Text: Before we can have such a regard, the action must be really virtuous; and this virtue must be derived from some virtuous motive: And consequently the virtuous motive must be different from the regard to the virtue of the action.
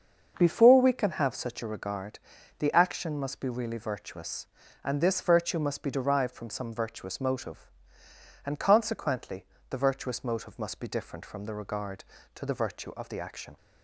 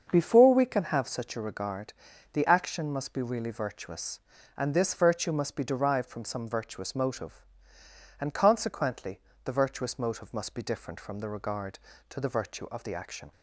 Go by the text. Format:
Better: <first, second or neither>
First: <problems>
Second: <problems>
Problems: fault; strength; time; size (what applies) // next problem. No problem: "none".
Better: neither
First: starts louder than the rest; until 1.3 s; 6.5 dB // pauses between "consequently" and "the"; slight; at 9.4 s; 0.24 s long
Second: starts louder than the rest; until 1.1 s; 6.5 dB // pauses between "consequently" and "the"; slight; at 9.1 s; 0.24 s long